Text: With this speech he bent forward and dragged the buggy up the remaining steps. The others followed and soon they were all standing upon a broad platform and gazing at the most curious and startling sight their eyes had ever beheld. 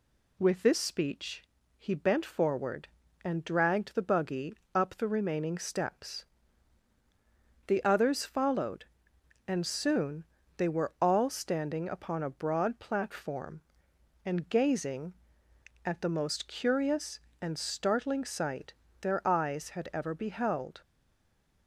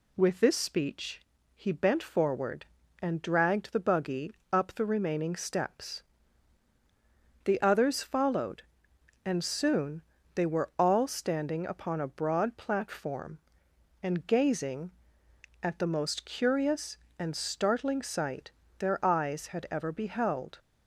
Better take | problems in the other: second | pauses between "speech" and "he"; slight; at 1.4 s; 0.36 s long; slight in the second // pauses between "buggy" and "up"; slight; at 4.5 s; 0.22 s long; slight in the second // pauses between "soon" and "they"; slight; at 10.2 s; 0.32 s long; slight in the second // pauses between "sight" and "their"; slight; at 18.7 s; 0.28 s long; slight in the second // stays silent after the last word; slight; from 20.8 s on; 0.8 s long

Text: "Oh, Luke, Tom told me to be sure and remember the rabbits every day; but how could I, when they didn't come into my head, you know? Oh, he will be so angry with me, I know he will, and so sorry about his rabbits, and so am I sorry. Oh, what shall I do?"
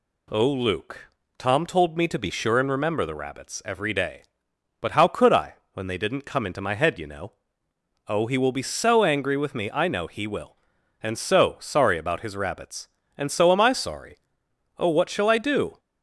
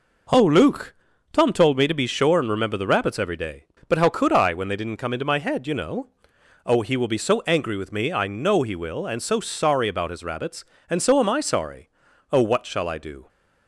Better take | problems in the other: neither | none

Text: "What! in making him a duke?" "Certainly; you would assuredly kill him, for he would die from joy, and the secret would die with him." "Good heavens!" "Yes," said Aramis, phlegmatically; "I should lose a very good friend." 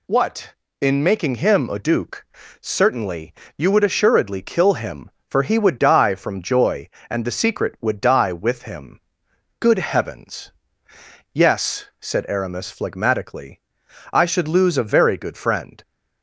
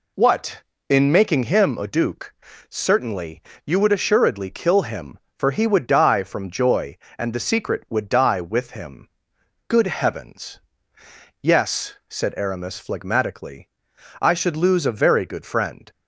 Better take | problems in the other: first | starts louder than the rest; slight; until 1.7 s; 2.5 dB

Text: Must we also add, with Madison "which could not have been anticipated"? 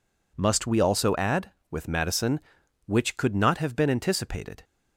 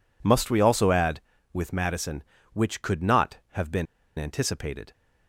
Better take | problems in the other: first | pauses between "been" and "anticipated"; slight; at 3.8 s; 0.32 s long

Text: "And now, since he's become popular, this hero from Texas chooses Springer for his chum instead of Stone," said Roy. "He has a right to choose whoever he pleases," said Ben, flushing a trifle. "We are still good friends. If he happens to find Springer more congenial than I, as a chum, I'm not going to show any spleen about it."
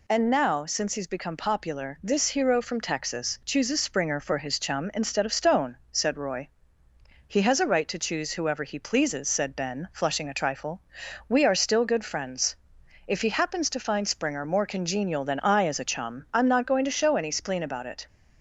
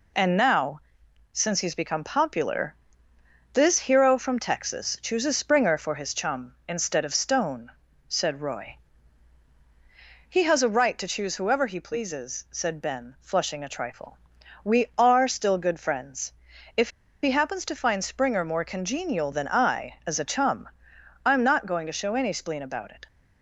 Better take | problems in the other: first | pauses between "If" and "he"; slight; at 16.9 s; 0.32 s long

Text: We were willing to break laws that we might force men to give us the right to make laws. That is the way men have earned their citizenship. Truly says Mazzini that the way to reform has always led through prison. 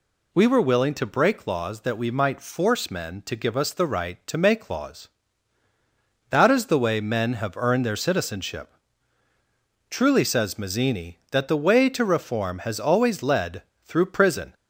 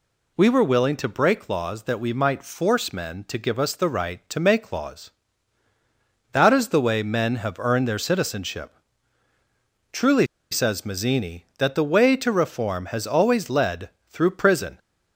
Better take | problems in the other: first | pauses between "Truly" and "says"; slight; at 10.2 s; 0.25 s long // pauses between "led" and "through"; slight; at 13.9 s; 0.20 s long; slight in the first

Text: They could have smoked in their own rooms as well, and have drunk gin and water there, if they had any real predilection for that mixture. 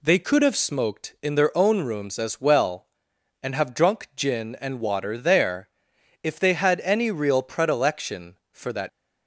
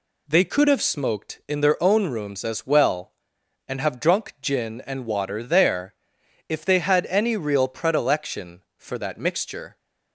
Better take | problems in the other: second | stops before "mixture"; at 8.8 s

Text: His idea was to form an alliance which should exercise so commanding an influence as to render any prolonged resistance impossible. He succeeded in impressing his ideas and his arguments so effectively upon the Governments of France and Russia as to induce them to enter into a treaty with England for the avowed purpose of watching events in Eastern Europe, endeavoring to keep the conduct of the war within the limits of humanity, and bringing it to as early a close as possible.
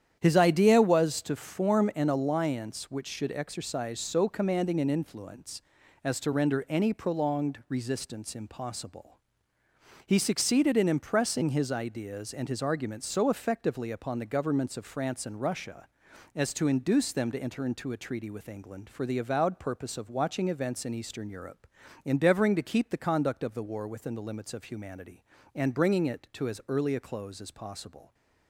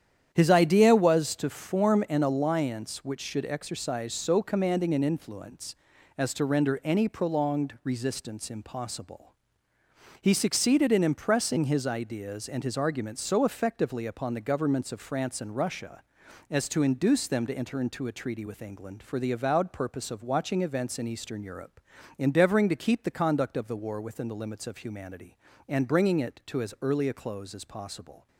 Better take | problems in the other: neither | starts louder than the rest; strong; the same in both

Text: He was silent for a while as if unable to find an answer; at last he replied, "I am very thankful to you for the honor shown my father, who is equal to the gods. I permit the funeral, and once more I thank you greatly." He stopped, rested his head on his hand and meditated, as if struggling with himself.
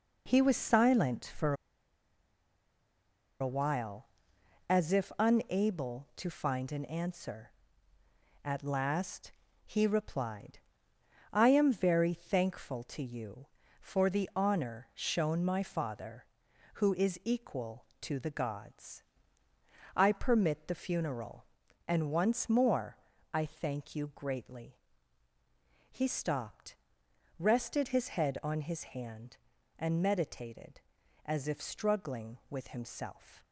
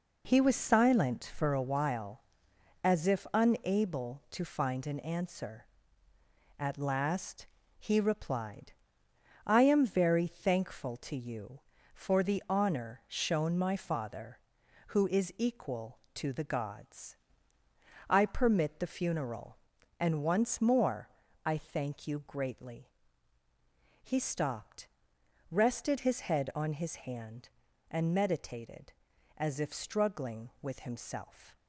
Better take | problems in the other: second | pauses between "for" and "a"; strong; at 1.5 s; 1.8 s long // pauses between "last" and "he"; slight; at 9.3 s; 0.34 s long; slight in the second // pauses between "more" and "I"; slight; at 22.9 s; 0.34 s long; slight in the second

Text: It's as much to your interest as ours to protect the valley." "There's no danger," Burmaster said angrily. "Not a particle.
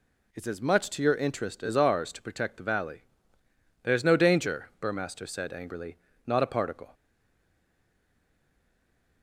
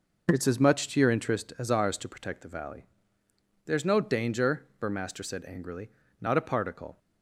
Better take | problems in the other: second | stays silent after the last word; from 6.9 s on; 2.3 s long

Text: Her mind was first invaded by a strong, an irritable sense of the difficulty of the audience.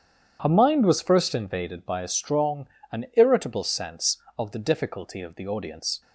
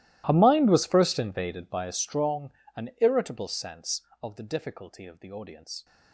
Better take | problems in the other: first | gets quieter; strong; throughout; 22 dB // starts louder than the rest; strong; until 1.2 s; 15.5 dB; strong in the first

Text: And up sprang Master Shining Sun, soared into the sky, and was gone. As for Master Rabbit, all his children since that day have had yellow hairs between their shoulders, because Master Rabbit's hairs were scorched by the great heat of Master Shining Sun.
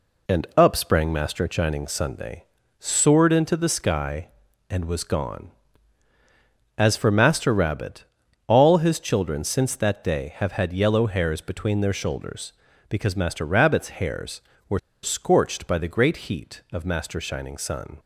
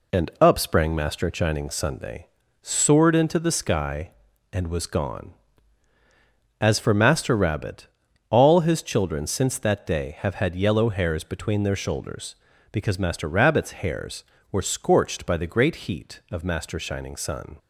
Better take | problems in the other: second | pauses between "were" and "scorched"; slight; at 14.7 s; 0.23 s long

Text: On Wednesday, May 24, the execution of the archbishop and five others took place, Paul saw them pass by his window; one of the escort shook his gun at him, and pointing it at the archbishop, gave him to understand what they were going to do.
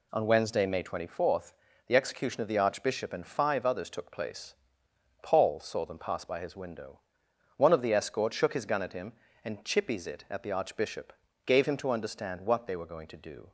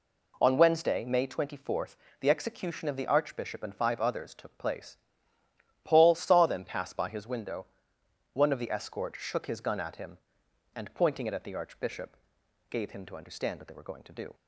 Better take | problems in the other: second | says "chippies" for "pointing"; at 9.6 s

